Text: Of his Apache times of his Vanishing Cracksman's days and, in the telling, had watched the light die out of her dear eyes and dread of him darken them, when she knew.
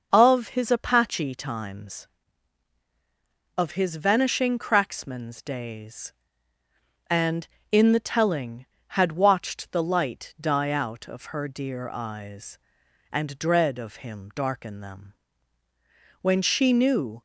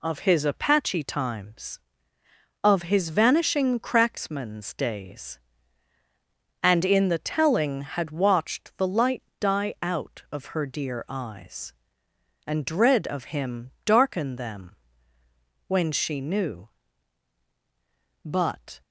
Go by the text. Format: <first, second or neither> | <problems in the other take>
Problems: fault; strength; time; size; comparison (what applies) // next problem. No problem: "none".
first | pauses between "light" and "die"; slight; at 9.2 s; 0.16 s long // pauses between "him" and "darken"; slight; at 13.7 s; 0.16 s long // goes on to say "But"; from 18.2 s on; 0.58 s long